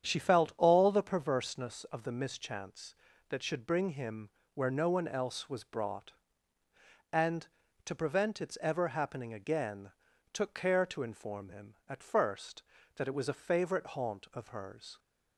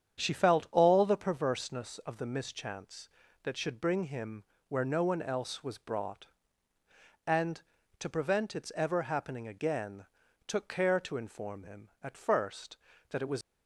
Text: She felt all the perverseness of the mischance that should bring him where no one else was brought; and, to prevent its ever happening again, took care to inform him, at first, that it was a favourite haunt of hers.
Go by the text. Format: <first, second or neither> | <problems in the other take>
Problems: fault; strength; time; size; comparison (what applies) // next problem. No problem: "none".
first | starts louder than the rest; strong; until 1.2 s; 8.5 dB; strong in the first // pauses between "him" and "where"; slight; at 4.4 s; 0.24 s long; slight in the first // stops before "a favourite haunt of hers"; at 13.4 s